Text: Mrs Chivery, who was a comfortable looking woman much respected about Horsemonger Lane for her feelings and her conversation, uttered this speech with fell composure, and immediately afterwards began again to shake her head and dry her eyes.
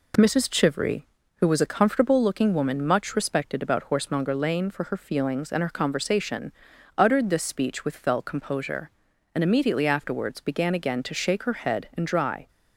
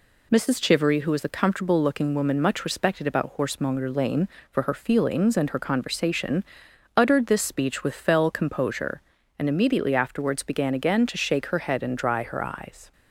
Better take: second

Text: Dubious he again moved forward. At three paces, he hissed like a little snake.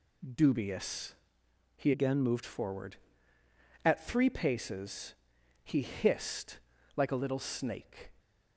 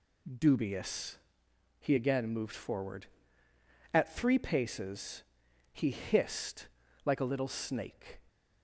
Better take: second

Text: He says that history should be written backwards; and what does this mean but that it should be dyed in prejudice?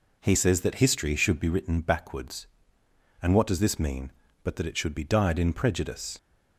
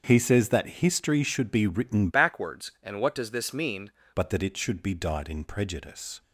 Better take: first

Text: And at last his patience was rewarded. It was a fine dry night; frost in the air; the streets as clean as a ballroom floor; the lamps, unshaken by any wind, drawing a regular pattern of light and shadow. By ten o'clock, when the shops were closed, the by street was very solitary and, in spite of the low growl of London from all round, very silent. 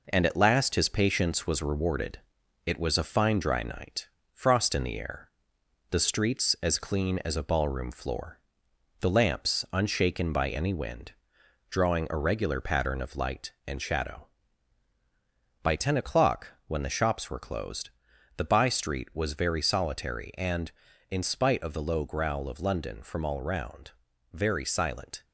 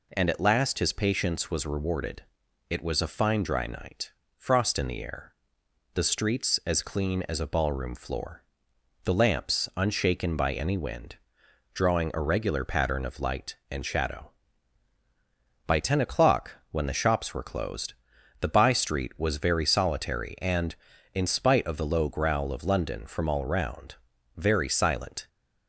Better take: second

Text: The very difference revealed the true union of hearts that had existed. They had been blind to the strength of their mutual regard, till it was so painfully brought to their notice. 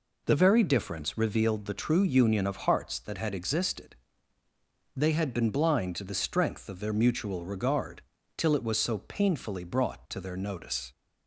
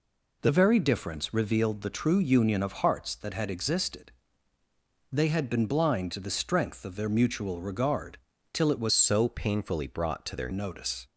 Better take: first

